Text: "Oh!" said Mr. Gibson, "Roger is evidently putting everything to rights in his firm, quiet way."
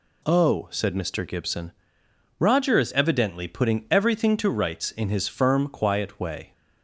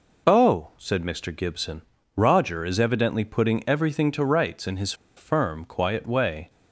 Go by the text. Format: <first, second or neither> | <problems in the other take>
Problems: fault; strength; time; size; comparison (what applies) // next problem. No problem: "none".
first | pauses between "his" and "firm"; slight; at 4.9 s; 0.23 s long